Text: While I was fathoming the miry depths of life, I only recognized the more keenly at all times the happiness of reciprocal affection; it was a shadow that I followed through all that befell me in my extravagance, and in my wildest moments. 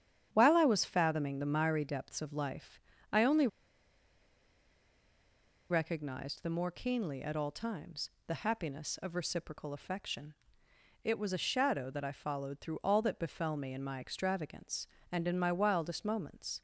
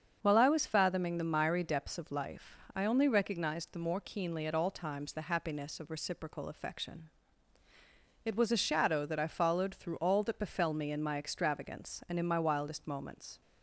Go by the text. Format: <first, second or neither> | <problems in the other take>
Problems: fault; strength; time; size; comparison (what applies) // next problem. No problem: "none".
second | starts louder than the rest; strong; until 1.3 s; 9.5 dB; also in the second // pauses between "only" and "recognized"; strong; at 3.4 s; 2.2 s long // pauses between "times" and "the"; slight; at 8.0 s; 0.18 s long